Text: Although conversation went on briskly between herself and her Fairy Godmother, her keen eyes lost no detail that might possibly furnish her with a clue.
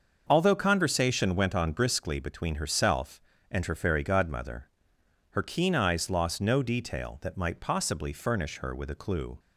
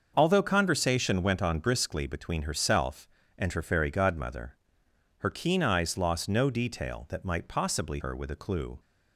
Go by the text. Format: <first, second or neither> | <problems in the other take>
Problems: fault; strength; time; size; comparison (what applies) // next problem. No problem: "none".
first | starts louder than the rest; until 1.1 s; 6.5 dB; also in the first // skips "furnish"; at 7.9 s